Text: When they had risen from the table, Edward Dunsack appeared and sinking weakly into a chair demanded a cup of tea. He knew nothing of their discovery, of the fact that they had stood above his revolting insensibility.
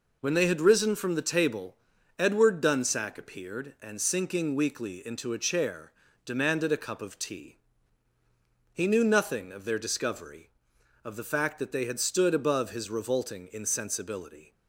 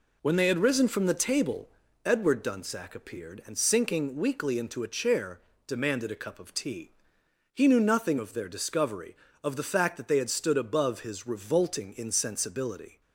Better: neither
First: pauses between "chair" and "demanded"; slight; at 5.9 s; 0.32 s long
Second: pauses between "chair" and "demanded"; slight; at 5.4 s; 0.28 s long

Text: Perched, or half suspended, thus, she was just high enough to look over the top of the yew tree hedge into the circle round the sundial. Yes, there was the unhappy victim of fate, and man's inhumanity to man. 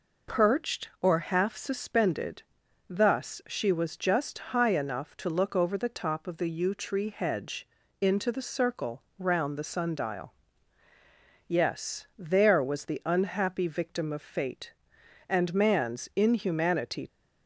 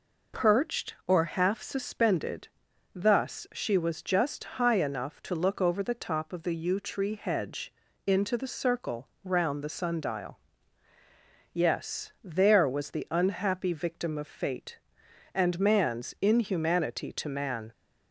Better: second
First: pauses between "just" and "high"; slight; at 4.3 s; 0.16 s long // pauses between "hedge" and "into"; slight; at 7.6 s; 0.32 s long // pauses between "circle" and "round"; slight; at 9.0 s; 0.16 s long // stops before "to man"; at 17.0 s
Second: pauses between "just" and "high"; slight; at 4.4 s; 0.16 s long // pauses between "hedge" and "into"; slight; at 7.7 s; 0.32 s long // pauses between "circle" and "round"; slight; at 9.0 s; 0.16 s long

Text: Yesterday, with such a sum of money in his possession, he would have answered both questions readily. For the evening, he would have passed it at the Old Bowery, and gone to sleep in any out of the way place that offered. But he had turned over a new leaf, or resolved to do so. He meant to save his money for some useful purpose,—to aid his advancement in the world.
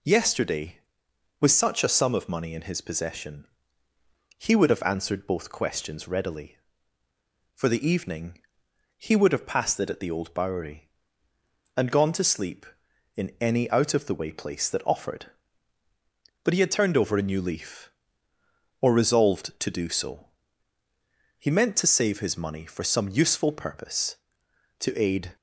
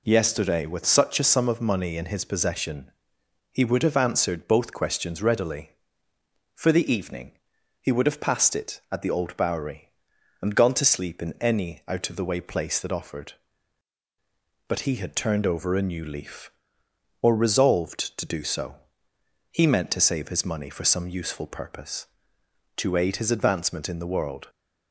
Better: second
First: stops before "his advancement in the world"; at 25.3 s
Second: none

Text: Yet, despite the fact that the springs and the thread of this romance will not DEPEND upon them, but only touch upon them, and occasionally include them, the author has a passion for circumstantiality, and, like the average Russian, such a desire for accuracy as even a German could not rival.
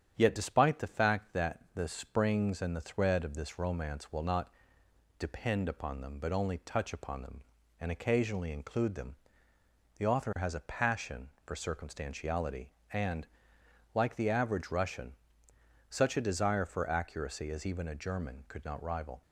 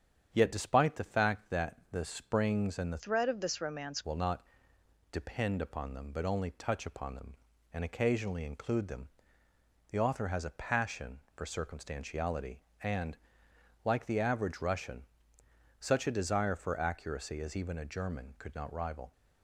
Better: first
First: starts louder than the rest; strong; until 1.1 s; 8.5 dB // pauses between "not" and "DEPEND"; noticeable; at 4.5 s; 0.68 s long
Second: starts louder than the rest; strong; until 1.3 s; 8 dB // changes voice from "thread" to "romance"; from 2.9 to 4.0 s; 1.1 s long // pauses between "not" and "DEPEND"; noticeable; at 4.4 s; 0.68 s long

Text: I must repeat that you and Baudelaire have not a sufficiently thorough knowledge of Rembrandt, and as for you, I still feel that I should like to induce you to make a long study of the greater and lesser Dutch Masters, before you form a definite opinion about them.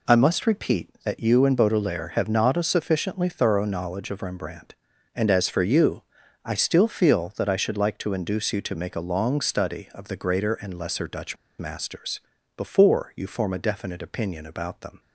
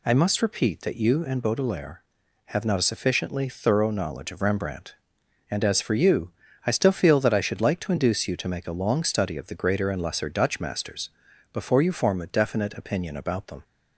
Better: second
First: pauses between "Dutch" and "Masters"; slight; at 11.3 s; 0.23 s long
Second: none

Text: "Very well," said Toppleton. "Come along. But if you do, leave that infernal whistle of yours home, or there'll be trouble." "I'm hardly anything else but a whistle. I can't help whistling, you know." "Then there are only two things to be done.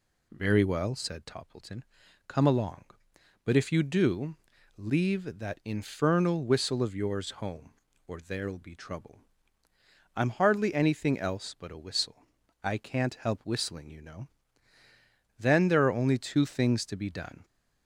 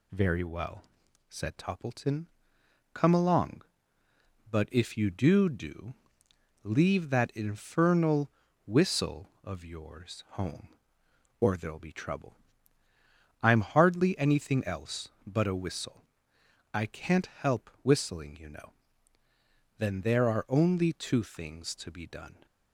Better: first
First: none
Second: says "do" twice; at 5.4 s // pauses between "infernal" and "whistle"; slight; at 8.3 s; 0.34 s long

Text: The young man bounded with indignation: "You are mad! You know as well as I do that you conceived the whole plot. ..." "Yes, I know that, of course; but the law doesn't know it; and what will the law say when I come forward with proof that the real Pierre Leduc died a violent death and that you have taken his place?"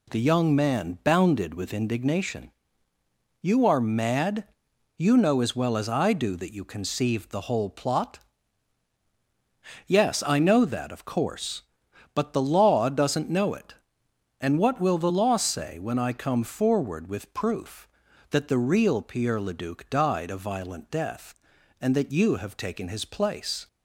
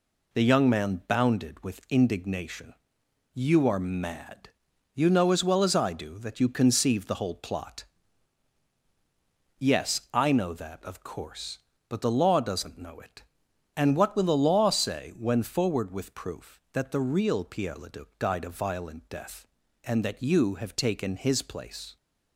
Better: first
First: none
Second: skips "I come"; at 15.4 s

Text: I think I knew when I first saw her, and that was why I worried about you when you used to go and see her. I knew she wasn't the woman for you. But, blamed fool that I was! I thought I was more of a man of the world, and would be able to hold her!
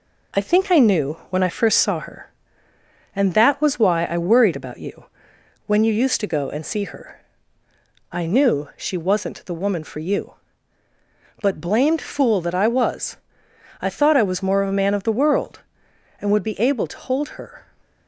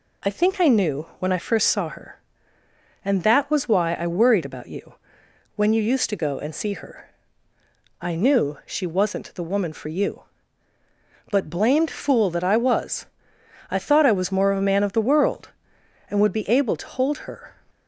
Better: second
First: gets quieter; slight; throughout; 2.5 dB // pauses between "you" and "when"; noticeable; at 5.0 s; 0.60 s long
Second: pauses between "you" and "when"; noticeable; at 4.9 s; 0.60 s long

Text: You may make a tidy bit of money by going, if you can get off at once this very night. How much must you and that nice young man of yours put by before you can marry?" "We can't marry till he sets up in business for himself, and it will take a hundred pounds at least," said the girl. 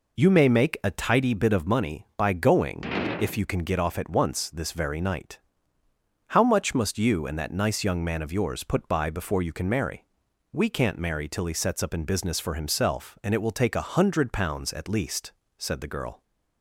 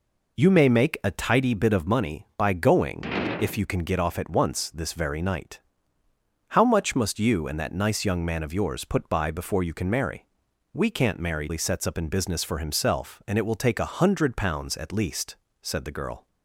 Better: first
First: none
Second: skips "till"; at 11.4 s

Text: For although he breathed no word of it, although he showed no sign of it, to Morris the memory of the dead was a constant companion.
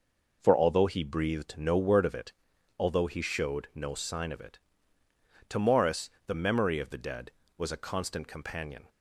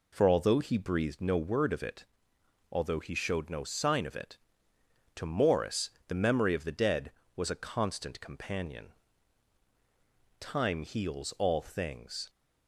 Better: first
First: pauses between "Morris" and "the"; slight; at 6.0 s; 0.18 s long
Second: pauses between "Morris" and "the"; slight; at 5.8 s; 0.16 s long // goes on to say "Time heals all things"; strong; from 10.3 s on; 1.9 s long

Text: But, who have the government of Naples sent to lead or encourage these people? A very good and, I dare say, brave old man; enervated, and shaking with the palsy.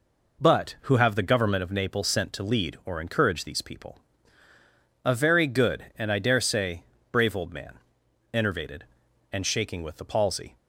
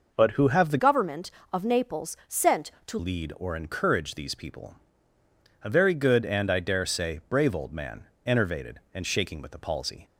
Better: first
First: none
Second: changes voice from "government" to "to"; from 0.7 to 2.9 s; 2.2 s long

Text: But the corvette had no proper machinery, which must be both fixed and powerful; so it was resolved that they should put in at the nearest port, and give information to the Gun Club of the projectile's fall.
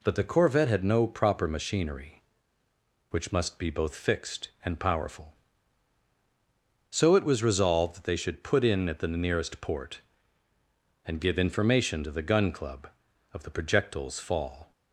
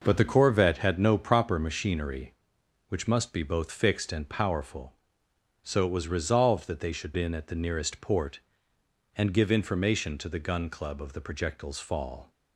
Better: first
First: none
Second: skips "put"; at 7.1 s

